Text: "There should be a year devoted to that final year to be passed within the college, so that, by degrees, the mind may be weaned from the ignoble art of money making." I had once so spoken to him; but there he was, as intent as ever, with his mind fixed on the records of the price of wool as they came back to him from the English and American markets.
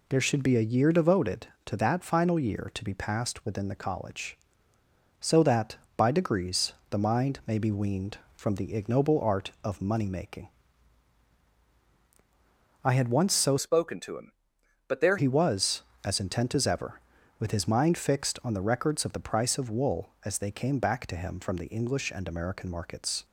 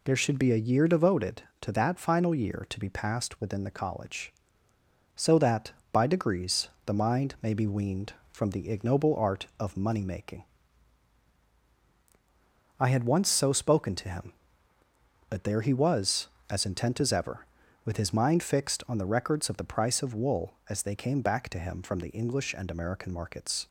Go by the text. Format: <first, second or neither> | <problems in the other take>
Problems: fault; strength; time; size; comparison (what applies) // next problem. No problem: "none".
second | changes voice from "spoken" to "there"; from 13.5 to 15.1 s; 1.6 s long